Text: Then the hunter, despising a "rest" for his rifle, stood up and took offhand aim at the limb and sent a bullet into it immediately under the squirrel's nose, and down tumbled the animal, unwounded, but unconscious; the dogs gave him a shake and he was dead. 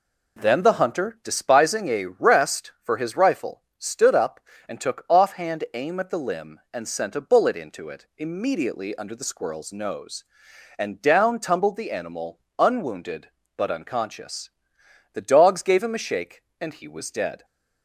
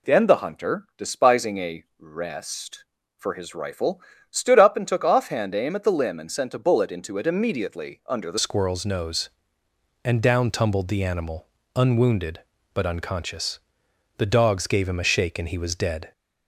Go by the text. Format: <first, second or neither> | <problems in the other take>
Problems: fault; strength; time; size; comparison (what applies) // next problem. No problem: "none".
first | pauses between "a" and "rest"; slight; at 1.8 s; 0.16 s long // changes voice at "squirrel's"; from 8.3 s on; 7.8 s long